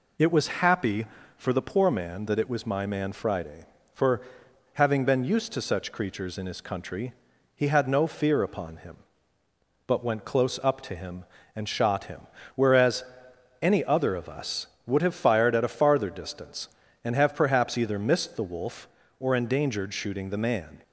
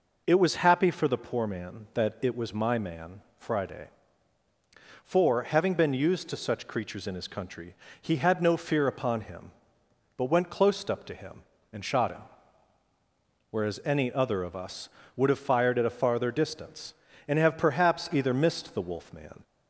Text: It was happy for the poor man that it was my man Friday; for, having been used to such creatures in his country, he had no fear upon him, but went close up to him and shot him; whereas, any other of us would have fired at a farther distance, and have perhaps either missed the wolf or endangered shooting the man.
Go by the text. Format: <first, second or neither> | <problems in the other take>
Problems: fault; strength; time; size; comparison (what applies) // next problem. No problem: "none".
first | pauses between "man" and "Friday"; slight; at 3.2 s; 0.18 s long // skips "or endangered shooting the"; at 19.1 s